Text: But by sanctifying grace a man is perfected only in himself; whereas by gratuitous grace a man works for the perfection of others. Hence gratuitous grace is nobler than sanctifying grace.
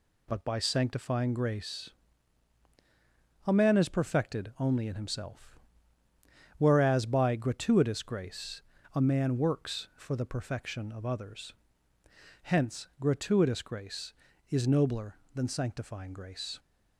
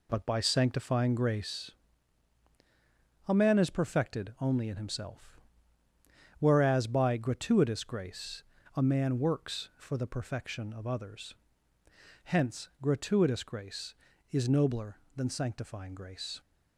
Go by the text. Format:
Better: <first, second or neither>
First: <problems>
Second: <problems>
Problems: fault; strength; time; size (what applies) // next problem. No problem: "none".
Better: first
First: pauses between "grace" and "a"; strong; at 1.8 s; 1.5 s long // pauses between "grace" and "a"; slight; at 8.6 s; 0.32 s long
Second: starts louder than the rest; slight; until 1.7 s; 2.5 dB // pauses between "grace" and "a"; strong; at 1.7 s; 1.5 s long // pauses between "grace" and "a"; slight; at 8.4 s; 0.32 s long